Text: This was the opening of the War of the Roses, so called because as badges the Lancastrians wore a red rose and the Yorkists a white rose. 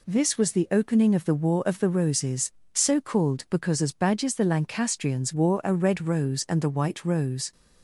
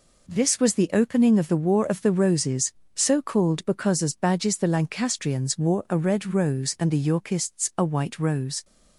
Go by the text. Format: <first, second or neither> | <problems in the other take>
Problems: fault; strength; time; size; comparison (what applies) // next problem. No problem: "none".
second | skips "Yorkists a"; at 6.6 s